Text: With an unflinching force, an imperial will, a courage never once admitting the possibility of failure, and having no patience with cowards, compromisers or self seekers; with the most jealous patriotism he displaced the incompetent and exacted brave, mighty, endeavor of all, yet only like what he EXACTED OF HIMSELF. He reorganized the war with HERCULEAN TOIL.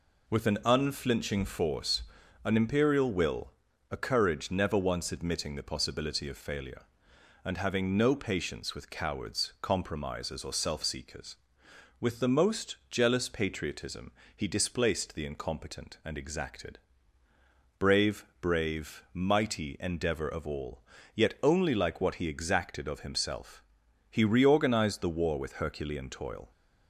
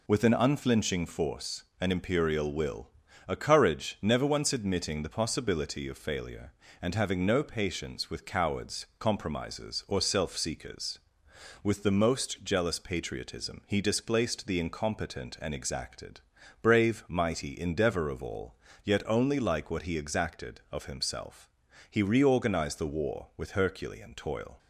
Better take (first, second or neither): second